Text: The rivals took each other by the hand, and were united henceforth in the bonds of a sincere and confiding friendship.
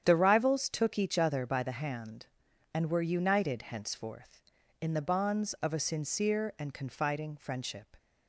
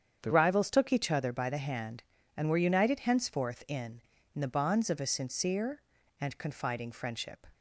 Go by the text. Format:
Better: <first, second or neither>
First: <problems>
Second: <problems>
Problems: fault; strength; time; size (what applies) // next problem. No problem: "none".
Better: first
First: starts louder than the rest; strong; until 1.0 s; 9 dB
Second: starts louder than the rest; strong; until 1.2 s; 8 dB // says "in" twice; at 4.3 s